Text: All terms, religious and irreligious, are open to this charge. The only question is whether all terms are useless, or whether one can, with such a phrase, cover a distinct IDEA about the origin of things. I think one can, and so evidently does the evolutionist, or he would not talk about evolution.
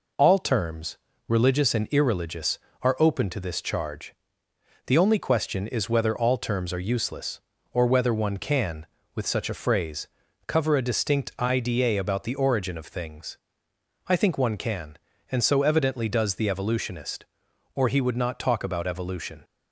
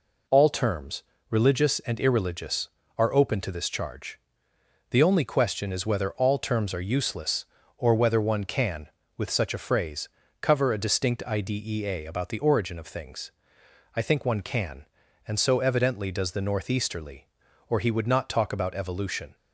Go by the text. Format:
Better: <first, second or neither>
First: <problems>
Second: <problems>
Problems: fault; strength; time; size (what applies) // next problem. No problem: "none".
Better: first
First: none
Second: says "northeasterly" for "evolutionist"; at 16.4 s